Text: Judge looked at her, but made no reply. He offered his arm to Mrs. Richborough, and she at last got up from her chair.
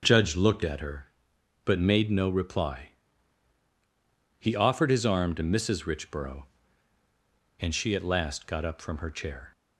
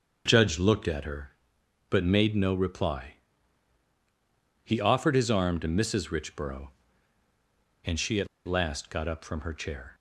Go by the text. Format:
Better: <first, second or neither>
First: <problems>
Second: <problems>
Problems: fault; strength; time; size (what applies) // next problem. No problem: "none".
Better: first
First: starts louder than the rest; until 1.0 s; 7 dB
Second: starts louder than the rest; until 1.2 s; 6.5 dB // pauses between "at" and "last"; slight; at 8.2 s; 0.19 s long